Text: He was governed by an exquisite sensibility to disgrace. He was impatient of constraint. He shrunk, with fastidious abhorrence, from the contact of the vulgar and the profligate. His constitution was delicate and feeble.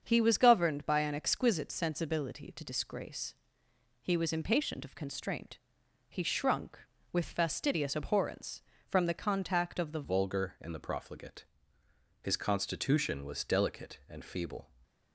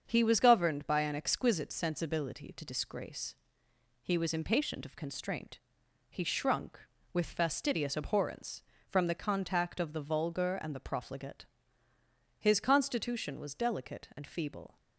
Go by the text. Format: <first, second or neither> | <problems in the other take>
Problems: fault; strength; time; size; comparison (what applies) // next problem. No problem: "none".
second | starts louder than the rest; until 1.0 s; 7 dB; also in the second // changes voice at "vulgar"; from 10.0 s on; 4.6 s long